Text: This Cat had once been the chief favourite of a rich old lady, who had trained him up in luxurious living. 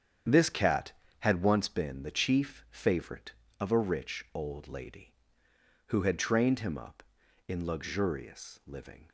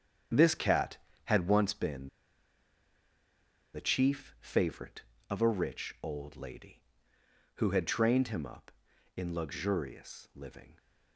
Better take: first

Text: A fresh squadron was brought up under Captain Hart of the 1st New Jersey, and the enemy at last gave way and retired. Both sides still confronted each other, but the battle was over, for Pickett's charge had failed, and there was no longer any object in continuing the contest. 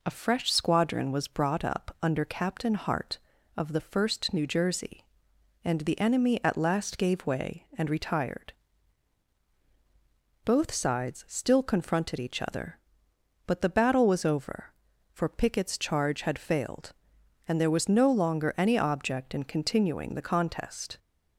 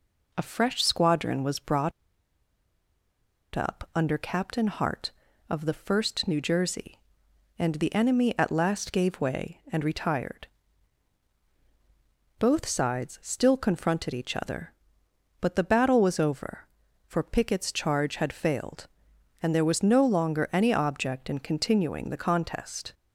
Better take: first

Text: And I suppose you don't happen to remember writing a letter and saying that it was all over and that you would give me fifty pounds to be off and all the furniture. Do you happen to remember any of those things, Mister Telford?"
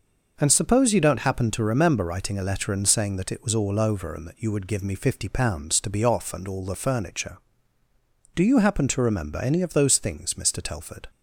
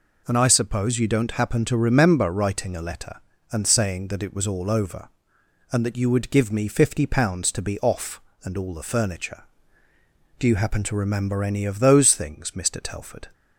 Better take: second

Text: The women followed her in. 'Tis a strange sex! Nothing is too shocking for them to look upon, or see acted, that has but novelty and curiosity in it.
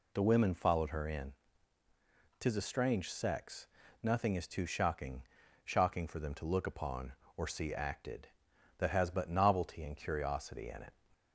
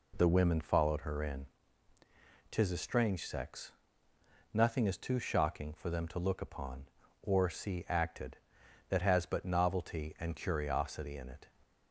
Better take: second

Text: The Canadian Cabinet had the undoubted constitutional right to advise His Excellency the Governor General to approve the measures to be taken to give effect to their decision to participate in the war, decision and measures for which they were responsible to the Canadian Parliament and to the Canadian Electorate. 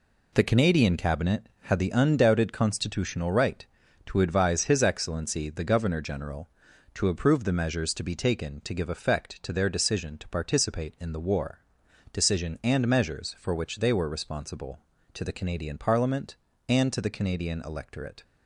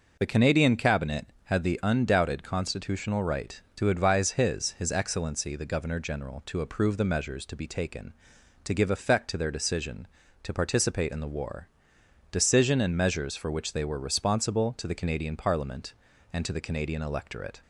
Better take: first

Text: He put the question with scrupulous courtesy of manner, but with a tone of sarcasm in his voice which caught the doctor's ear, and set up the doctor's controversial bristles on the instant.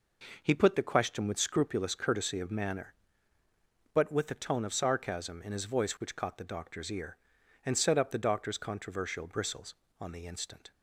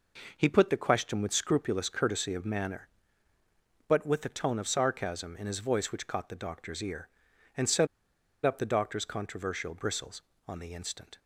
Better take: first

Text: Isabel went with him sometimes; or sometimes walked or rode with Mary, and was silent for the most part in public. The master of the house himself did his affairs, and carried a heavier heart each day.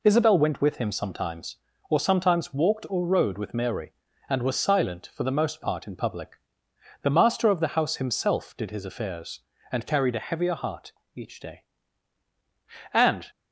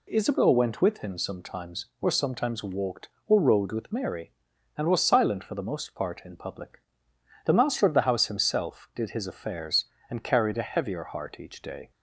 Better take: second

